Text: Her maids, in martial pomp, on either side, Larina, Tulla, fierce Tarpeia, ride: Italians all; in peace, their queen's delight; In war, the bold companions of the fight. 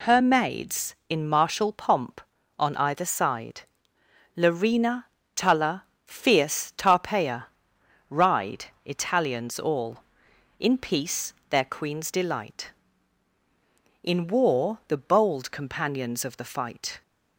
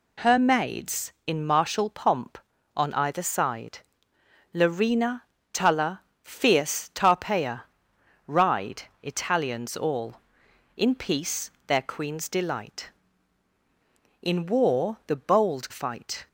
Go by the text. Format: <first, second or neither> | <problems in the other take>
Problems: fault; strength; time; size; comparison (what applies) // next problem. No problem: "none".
first | skips "companions of the"; at 15.7 s